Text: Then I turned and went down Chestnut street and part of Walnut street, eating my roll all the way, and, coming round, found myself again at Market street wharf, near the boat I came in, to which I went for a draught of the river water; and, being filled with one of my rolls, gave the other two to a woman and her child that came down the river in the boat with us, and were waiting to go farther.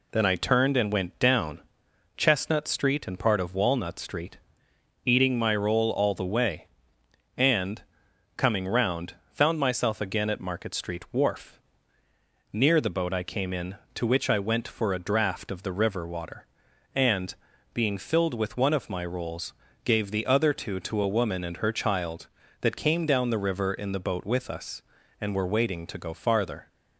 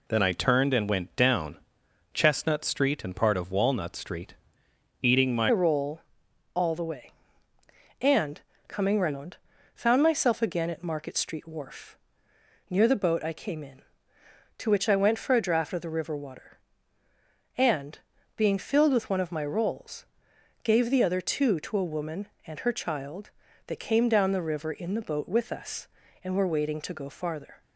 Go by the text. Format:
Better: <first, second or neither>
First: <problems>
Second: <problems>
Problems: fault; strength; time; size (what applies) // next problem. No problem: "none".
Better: first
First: pauses between "down" and "Chestnut"; noticeable; at 1.5 s; 0.58 s long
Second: pauses between "down" and "Chestnut"; noticeable; at 1.5 s; 0.58 s long // changes voice at "roll"; from 5.5 s on; 22.1 s long // pauses between "roll" and "all"; noticeable; at 6.0 s; 0.52 s long